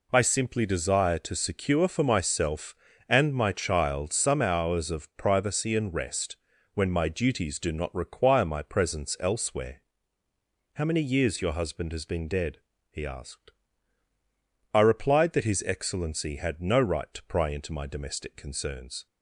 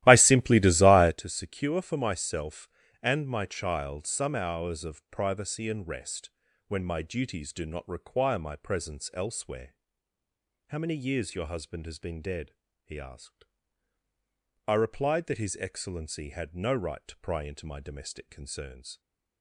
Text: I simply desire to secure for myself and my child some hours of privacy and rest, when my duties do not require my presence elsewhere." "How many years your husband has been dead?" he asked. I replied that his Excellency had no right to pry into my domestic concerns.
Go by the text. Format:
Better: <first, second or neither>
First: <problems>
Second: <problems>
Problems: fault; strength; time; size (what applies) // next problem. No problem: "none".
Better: first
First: none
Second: starts louder than the rest; strong; until 1.2 s; 15 dB